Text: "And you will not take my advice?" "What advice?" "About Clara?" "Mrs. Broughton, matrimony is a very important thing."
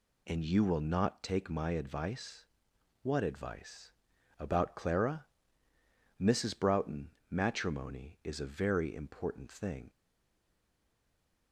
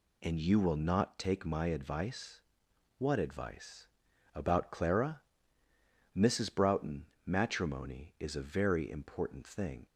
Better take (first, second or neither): second